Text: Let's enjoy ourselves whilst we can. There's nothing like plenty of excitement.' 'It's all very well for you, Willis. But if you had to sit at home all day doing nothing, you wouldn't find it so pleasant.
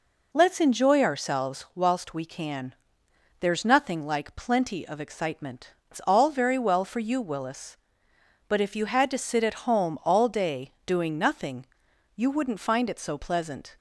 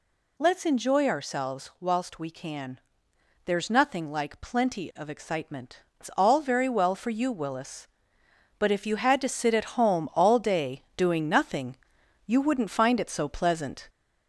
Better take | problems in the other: first | gets louder; slight; throughout; 2 dB // pauses between "day" and "doing"; slight; at 10.8 s; 0.16 s long; slight in the first

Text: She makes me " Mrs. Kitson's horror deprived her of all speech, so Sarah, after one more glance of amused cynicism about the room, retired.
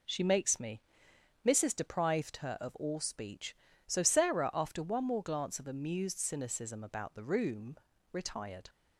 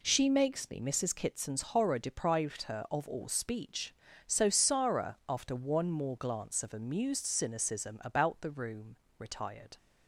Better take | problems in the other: second | skips "Kitson's horror"; at 1.7 s

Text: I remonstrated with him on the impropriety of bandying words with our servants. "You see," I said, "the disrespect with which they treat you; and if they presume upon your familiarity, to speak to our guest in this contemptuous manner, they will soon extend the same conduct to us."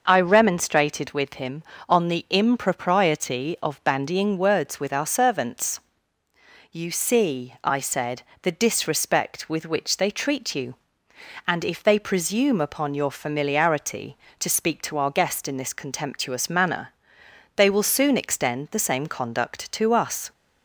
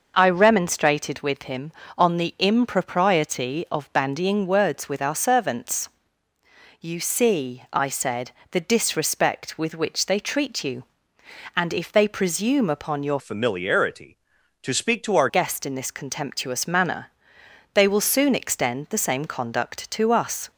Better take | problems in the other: first | changes voice from "familiarity" to "our"; from 13.1 to 15.2 s; 2.1 s long

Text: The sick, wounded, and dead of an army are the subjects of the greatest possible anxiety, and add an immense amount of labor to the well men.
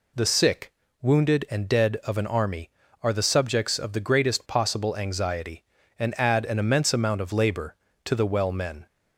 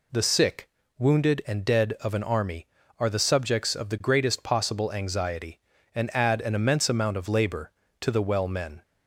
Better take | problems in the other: neither | none

